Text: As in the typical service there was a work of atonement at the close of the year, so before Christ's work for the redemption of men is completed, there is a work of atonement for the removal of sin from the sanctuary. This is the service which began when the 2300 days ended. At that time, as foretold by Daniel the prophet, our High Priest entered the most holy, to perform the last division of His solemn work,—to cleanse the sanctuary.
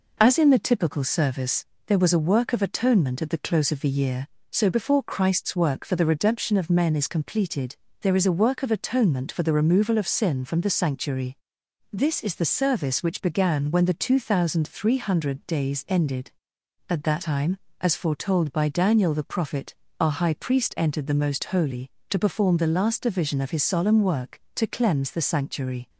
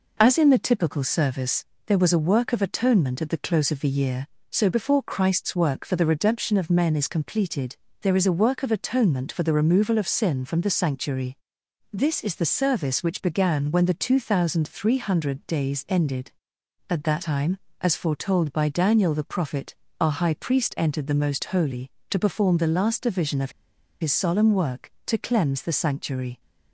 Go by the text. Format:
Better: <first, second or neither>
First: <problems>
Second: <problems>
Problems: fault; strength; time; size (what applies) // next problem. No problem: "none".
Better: first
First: pauses between "service" and "there"; slight; at 1.6 s; 0.22 s long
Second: pauses between "service" and "there"; slight; at 1.6 s; 0.22 s long // pauses between "of" and "His"; noticeable; at 23.5 s; 0.49 s long